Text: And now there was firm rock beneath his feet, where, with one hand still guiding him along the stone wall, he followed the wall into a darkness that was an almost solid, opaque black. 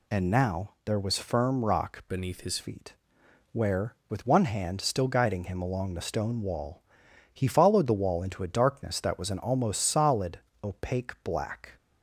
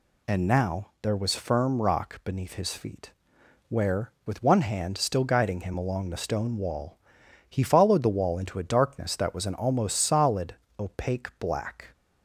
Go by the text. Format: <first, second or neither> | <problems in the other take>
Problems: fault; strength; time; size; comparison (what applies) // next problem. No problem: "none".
second | changes voice from "beneath" to "his"; from 2.0 to 2.5 s; 0.5 s long